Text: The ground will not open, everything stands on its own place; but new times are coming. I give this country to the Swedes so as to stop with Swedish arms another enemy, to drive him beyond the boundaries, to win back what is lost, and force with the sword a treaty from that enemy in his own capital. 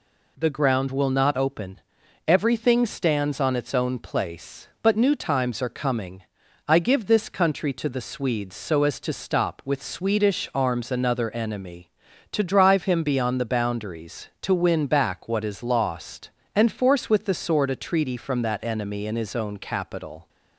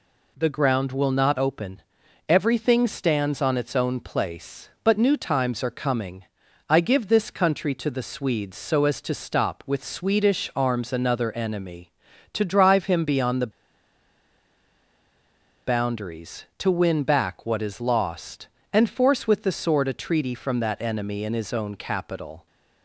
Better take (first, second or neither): first